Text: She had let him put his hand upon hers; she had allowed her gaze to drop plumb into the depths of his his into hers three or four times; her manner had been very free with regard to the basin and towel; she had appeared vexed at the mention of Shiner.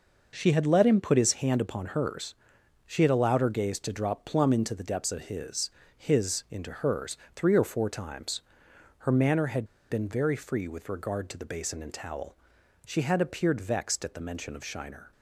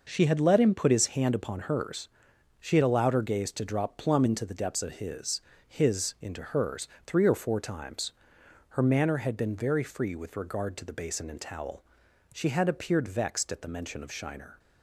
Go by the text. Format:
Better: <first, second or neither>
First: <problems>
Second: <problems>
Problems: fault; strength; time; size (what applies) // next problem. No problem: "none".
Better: second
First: pauses between "his" and "his"; slight; at 5.6 s; 0.26 s long // pauses between "hers" and "three"; slight; at 7.1 s; 0.20 s long // pauses between "had" and "been"; slight; at 9.6 s; 0.26 s long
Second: pauses between "his" and "his"; slight; at 5.4 s; 0.26 s long // pauses between "hers" and "three"; slight; at 6.8 s; 0.20 s long